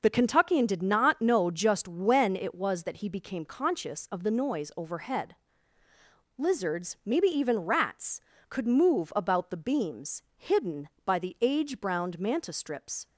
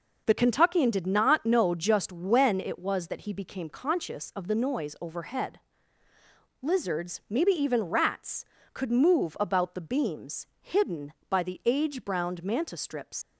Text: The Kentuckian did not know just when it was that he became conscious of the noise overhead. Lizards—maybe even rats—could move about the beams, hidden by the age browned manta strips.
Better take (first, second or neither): first